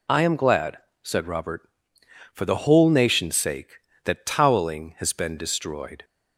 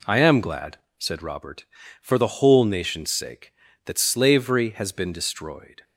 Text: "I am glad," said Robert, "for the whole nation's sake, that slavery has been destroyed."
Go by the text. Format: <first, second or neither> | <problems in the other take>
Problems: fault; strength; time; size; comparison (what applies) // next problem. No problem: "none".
second | says "toweling" for "slavery"; at 4.2 s